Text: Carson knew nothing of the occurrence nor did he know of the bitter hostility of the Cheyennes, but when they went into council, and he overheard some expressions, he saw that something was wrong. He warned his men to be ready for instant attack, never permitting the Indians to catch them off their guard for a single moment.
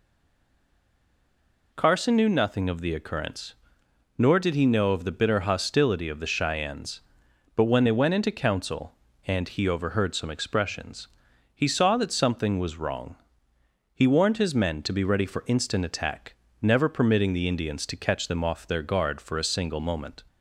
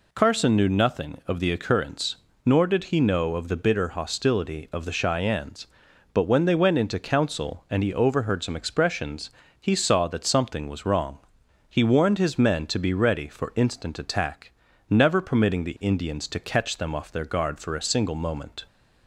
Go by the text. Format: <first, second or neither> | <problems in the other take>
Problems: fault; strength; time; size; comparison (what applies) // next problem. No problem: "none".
second | stays silent before the first word; noticeable; until 1.7 s; 1.7 s long // pauses between "occurrence" and "nor"; noticeable; at 3.5 s; 0.64 s long; slight in the second